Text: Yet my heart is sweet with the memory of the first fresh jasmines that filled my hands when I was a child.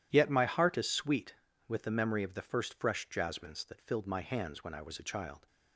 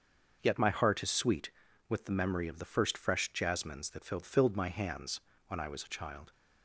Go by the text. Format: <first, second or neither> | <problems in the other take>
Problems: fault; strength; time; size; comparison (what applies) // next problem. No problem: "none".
first | starts louder than the rest; until 1.4 s; 6.5 dB // says "filled" twice; at 4.2 s // pauses between "hands" and "when"; slight; at 5.1 s; 0.28 s long